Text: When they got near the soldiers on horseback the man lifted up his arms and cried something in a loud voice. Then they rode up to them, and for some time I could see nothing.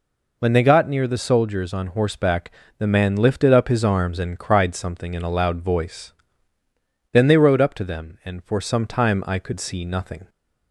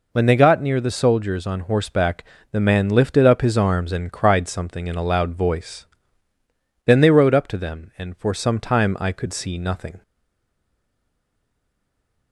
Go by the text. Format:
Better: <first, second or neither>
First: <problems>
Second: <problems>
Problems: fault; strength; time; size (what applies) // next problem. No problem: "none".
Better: first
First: pauses between "horseback" and "the"; slight; at 2.5 s; 0.26 s long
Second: pauses between "horseback" and "the"; slight; at 2.2 s; 0.26 s long // stays silent after the last word; from 10.0 s on; 2.3 s long